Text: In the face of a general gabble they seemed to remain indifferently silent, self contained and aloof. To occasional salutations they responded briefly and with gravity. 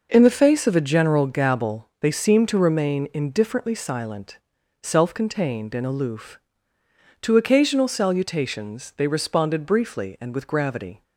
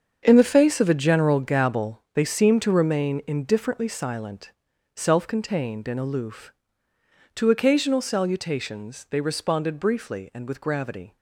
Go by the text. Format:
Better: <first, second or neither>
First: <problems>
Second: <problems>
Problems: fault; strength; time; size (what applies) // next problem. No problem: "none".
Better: first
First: none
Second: gets quieter; strong; throughout; 11.5 dB